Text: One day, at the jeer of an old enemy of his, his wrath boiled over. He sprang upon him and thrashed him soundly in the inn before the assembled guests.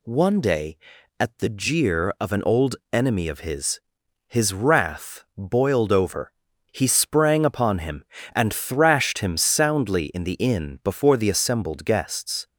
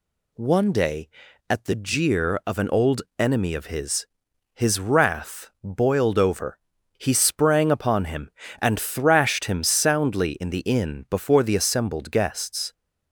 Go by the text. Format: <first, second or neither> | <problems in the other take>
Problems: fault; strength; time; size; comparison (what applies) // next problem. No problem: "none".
neither | pauses between "old" and "enemy"; slight; the same in both